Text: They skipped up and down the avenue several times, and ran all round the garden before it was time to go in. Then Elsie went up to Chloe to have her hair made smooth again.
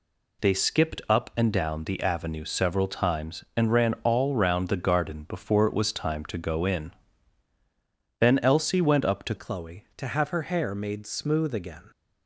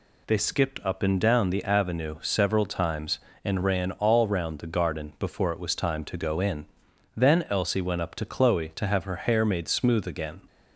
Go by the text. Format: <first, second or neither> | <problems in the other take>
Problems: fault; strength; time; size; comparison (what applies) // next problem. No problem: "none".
second | changes voice at "Chloe"; from 9.3 s on; 2.6 s long